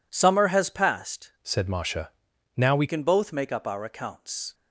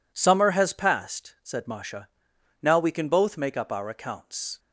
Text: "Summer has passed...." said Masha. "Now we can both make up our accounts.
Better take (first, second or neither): second